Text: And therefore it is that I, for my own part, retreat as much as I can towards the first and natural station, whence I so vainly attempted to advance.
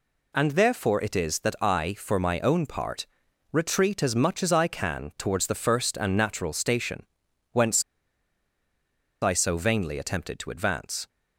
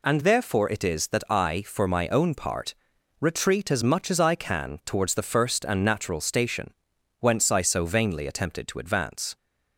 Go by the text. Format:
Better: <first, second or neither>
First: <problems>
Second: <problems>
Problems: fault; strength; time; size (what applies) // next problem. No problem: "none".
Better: second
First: pauses between "whence" and "I"; strong; at 7.8 s; 1.3 s long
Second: none